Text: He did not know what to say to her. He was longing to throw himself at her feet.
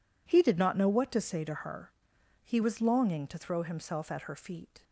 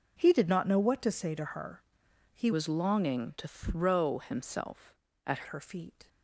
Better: first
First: none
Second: changes voice from "was" to "at"; from 2.5 to 5.4 s; 2.9 s long

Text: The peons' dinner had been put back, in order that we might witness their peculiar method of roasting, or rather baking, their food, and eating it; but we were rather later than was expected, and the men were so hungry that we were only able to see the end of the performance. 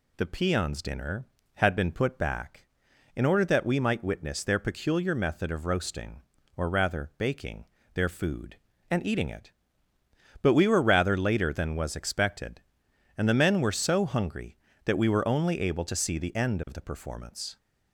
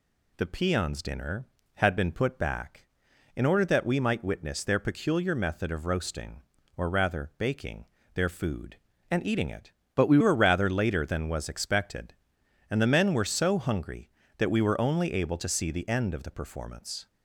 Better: first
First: none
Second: changes voice from "but" to "we"; from 9.9 to 10.1 s; 0.2 s long

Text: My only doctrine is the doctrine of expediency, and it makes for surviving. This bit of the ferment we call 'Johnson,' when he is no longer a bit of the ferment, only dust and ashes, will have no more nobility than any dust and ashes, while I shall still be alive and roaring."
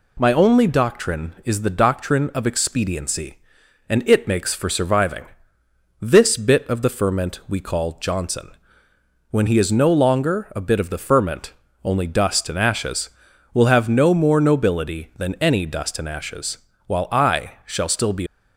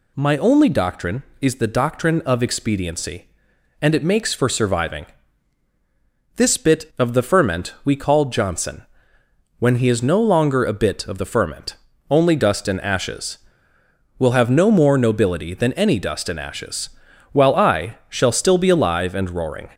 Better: second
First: pauses between "I" and "shall"; slight; at 17.5 s; 0.16 s long // stops before "alive and roaring"; at 18.2 s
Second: none

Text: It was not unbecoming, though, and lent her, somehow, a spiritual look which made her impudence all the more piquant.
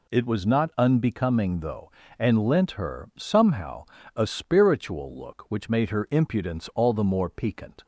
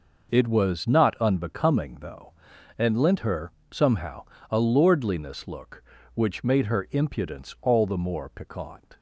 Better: first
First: none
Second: says "lordliness" for "spiritual"; at 4.6 s

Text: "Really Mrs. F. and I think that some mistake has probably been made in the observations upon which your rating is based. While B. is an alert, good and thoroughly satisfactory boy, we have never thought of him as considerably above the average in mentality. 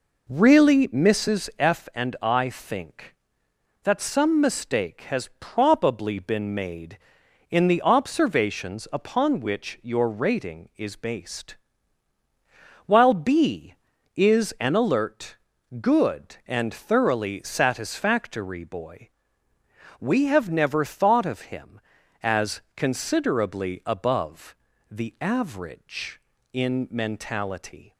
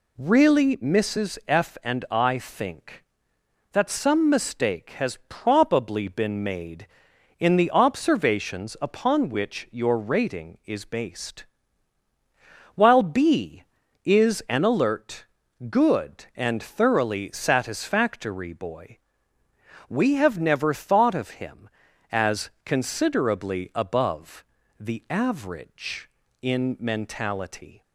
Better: second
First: starts louder than the rest; noticeable; until 1.8 s; 4 dB // pauses between "as" and "considerably"; slight; at 22.5 s; 0.16 s long // pauses between "above" and "the"; slight; at 24.5 s; 0.36 s long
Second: pauses between "as" and "considerably"; slight; at 22.4 s; 0.16 s long // pauses between "above" and "the"; slight; at 24.4 s; 0.36 s long

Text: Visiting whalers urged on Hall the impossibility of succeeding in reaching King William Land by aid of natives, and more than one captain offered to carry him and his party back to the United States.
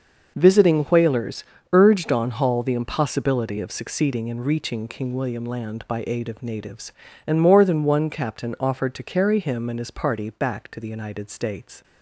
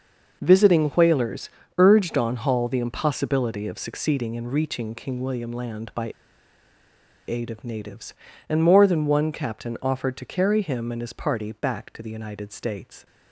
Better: first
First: starts louder than the rest; noticeable; until 1.3 s; 6 dB // pauses between "whalers" and "urged"; slight; at 1.4 s; 0.30 s long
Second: starts louder than the rest; noticeable; until 1.4 s; 6 dB // pauses between "whalers" and "urged"; slight; at 1.4 s; 0.30 s long // pauses between "by" and "aid"; at 6.1 s; 1.1 s long

